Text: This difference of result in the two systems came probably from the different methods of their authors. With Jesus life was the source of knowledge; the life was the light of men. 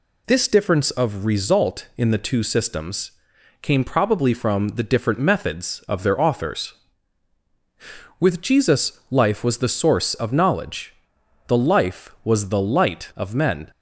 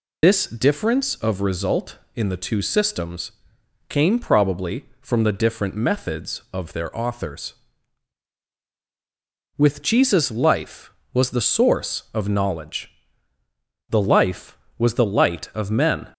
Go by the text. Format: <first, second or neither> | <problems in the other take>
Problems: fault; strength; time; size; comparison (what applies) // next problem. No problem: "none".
first | loses the start of "This"; at 0.2 s; 75 ms // pauses between "systems" and "came"; noticeable; at 3.3 s; 0.56 s long; noticeable in the first